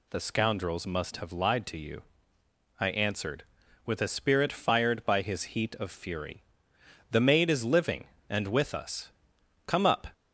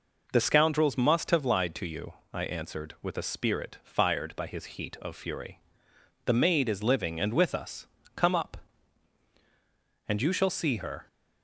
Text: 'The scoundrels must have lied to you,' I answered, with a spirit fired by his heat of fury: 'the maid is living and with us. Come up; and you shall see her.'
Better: second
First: stops before "and you shall see her"; at 10.1 s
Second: none

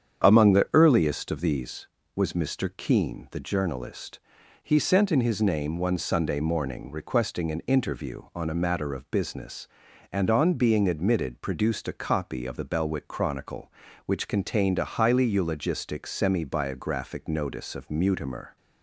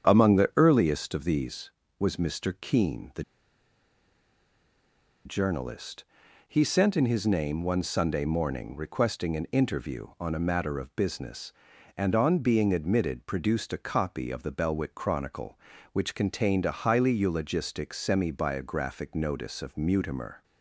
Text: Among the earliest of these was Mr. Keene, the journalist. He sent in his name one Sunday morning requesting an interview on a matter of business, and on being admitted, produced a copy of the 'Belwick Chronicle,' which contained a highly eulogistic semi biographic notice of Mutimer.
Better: first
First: starts louder than the rest; strong; until 1.2 s; 7.5 dB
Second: starts louder than the rest; strong; until 1.1 s; 7.5 dB // pauses between "the" and "journalist"; strong; at 3.2 s; 2.0 s long

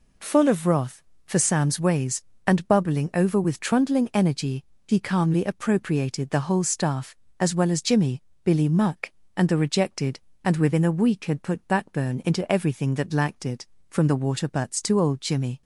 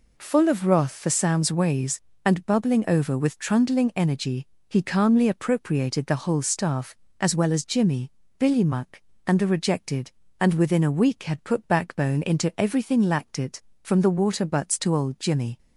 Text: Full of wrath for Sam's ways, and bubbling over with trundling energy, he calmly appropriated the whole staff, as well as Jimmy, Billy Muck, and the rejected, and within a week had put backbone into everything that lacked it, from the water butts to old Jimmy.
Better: first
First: none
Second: skips "that"; at 13.0 s

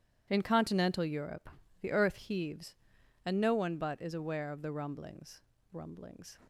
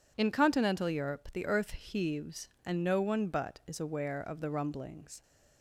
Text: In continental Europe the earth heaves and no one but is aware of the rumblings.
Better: second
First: pauses between "Europe" and "the"; slight; at 1.4 s; 0.32 s long // says "rumblings" twice; at 5.7 s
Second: none

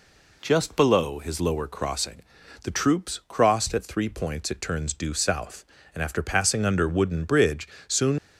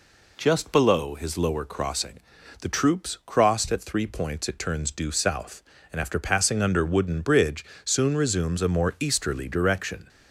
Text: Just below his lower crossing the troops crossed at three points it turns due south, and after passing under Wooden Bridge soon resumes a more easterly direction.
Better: second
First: pauses between "crossing" and "the"; at 2.2 s; 0.42 s long // pauses between "Bridge" and "soon"; slight; at 7.6 s; 0.20 s long // stops before "resumes a more easterly direction"; at 8.1 s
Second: pauses between "crossing" and "the"; at 2.1 s; 0.42 s long // pauses between "Bridge" and "soon"; slight; at 7.6 s; 0.20 s long

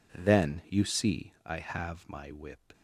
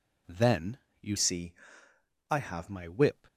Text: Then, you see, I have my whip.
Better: first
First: none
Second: changes voice from "see" to "have"; from 1.1 to 2.6 s; 1.5 s long

